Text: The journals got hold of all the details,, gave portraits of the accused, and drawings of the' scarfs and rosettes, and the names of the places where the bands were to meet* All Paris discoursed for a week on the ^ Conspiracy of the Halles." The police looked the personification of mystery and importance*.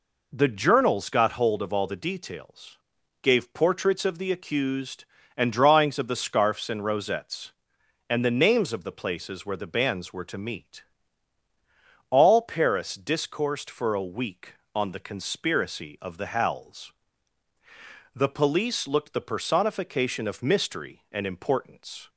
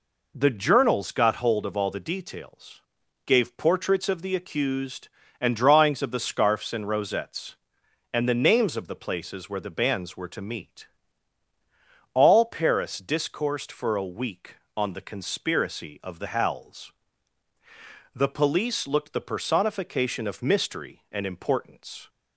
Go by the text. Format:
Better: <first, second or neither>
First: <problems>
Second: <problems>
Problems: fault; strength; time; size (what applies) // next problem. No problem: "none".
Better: neither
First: pauses between "meet" and "All"; strong; at 10.8 s; 1.2 s long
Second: pauses between "meet" and "All"; strong; at 10.8 s; 1.2 s long